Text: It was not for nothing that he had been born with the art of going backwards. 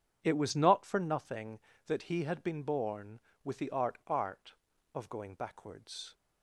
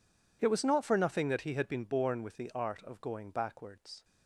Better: second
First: says "art" twice; at 4.0 s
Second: none

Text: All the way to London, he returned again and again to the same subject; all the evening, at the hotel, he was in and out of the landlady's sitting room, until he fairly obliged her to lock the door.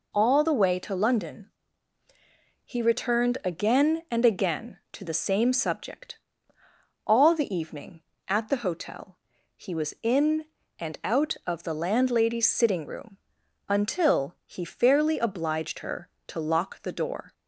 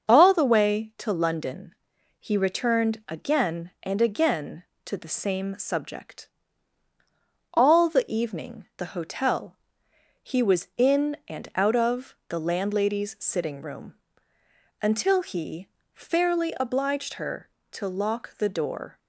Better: first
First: none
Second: starts louder than the rest; until 1.1 s; 6.5 dB // skips "at"; at 8.7 s // pauses between "he" and "fairly"; slight; at 15.6 s; 0.26 s long

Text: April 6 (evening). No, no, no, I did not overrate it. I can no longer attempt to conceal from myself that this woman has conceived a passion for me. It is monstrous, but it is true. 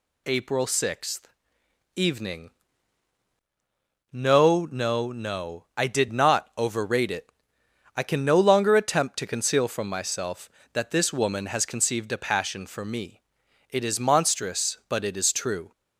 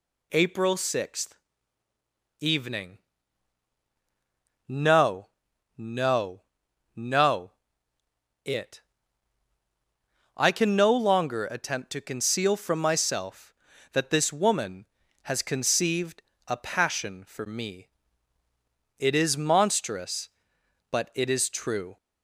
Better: first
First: none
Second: skips "I did not overrate"; at 7.9 s // pauses between "conceived" and "a"; slight; at 16.2 s; 0.24 s long

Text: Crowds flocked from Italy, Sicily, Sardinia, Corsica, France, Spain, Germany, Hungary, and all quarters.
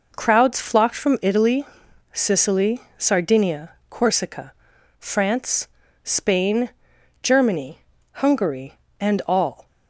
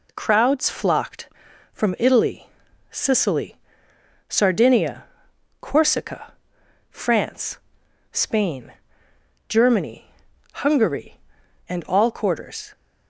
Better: second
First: stops before "quarters"; at 9.6 s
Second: none

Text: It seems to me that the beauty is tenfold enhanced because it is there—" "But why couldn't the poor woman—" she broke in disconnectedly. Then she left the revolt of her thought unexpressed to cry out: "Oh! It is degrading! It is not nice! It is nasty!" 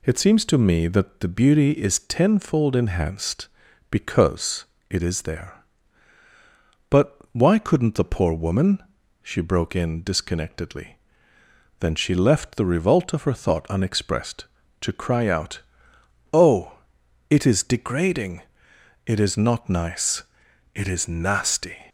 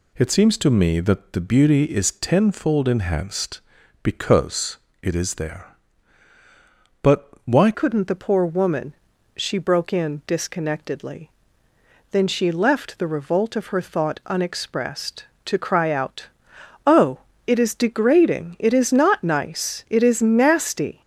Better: first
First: pauses between "because" and "it"; slight; at 4.6 s; 0.26 s long // pauses between "But" and "why"; slight; at 7.1 s; 0.18 s long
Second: pauses between "because" and "it"; slight; at 4.7 s; 0.26 s long // pauses between "But" and "why"; slight; at 7.2 s; 0.18 s long // changes voice at "couldn't"; from 7.7 s on; 13.3 s long

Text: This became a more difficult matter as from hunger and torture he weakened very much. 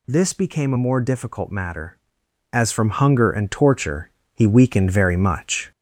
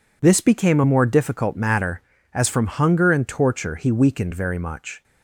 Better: second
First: gets louder; slight; throughout; 3 dB // pauses between "torture" and "he"; slight; at 4.0 s; 0.24 s long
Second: none

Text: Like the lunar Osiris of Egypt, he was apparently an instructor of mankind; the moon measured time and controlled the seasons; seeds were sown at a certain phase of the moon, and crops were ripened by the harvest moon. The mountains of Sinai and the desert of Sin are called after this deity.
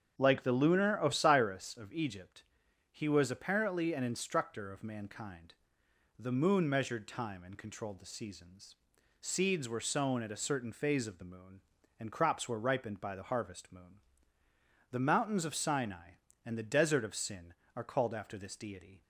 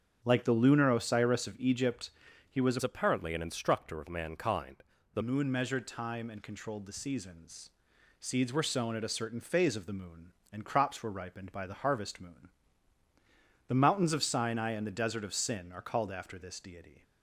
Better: first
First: starts louder than the rest; strong; until 1.1 s; 7.5 dB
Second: starts louder than the rest; strong; until 1.2 s; 8.5 dB // changes voice from "apparently" to "the"; from 2.8 to 5.2 s; 2.4 s long

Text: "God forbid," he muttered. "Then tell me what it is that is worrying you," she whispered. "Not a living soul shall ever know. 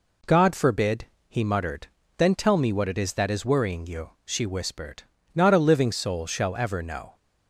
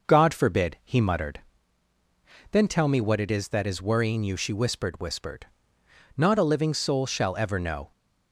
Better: first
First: none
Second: says "whispered" twice; at 4.9 s

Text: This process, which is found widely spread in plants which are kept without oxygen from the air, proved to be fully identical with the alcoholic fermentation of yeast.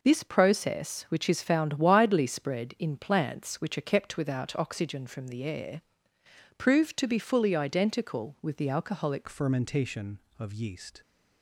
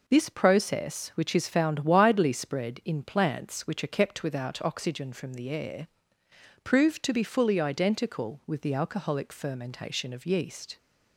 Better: second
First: changes voice at "fermentation"; from 9.2 s on; 1.8 s long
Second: none

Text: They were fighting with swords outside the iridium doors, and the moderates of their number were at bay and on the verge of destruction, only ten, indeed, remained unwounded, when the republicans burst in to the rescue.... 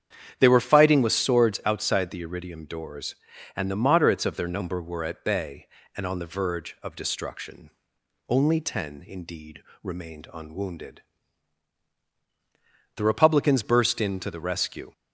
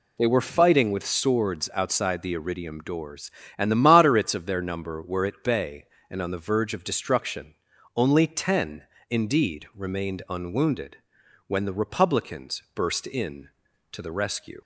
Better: second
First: starts louder than the rest; strong; until 1.3 s; 8.5 dB // skips "when"; at 11.9 s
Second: none

